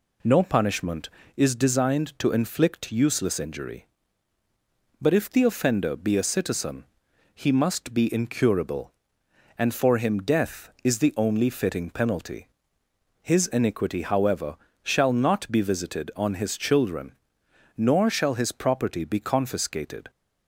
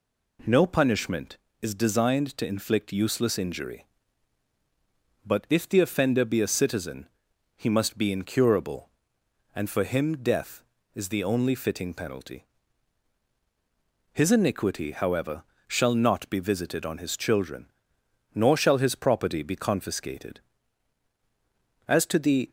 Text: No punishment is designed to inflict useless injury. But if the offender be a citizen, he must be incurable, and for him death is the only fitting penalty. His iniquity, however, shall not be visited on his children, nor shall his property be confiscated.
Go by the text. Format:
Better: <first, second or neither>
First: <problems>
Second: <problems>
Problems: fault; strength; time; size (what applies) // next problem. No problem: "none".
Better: first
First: none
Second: goes on to say "As to the"; noticeable; from 21.8 s on; 0.64 s long